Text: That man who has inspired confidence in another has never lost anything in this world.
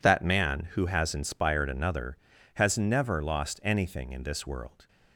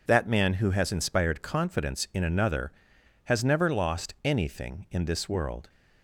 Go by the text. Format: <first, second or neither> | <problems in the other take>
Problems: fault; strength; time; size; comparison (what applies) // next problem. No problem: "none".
second | skips "confidence in"; at 1.6 s